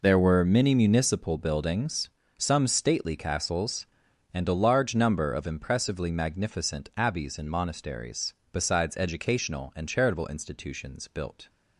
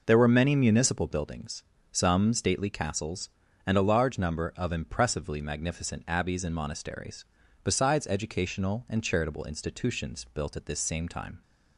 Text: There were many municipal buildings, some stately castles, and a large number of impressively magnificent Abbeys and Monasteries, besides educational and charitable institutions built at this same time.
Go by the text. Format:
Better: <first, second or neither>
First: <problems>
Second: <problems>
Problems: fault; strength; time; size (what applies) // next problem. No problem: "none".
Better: second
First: stops before "at this same time"; at 11.4 s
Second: none